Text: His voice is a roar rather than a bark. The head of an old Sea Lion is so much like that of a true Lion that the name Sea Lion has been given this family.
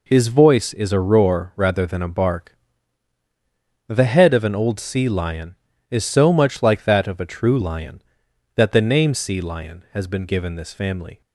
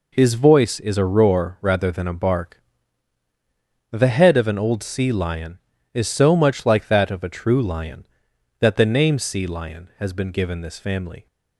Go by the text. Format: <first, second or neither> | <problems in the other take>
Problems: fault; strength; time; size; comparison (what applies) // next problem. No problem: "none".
neither | none